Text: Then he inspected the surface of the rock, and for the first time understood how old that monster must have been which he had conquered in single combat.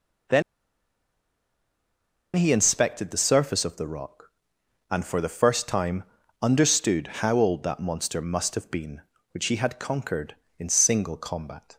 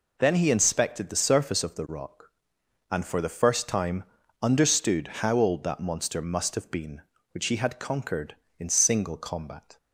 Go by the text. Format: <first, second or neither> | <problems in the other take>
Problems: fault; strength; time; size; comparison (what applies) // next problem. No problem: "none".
second | pauses between "Then" and "he"; strong; at 0.4 s; 1.9 s long // pauses between "time" and "understood"; slight; at 6.0 s; 0.36 s long; slight in the second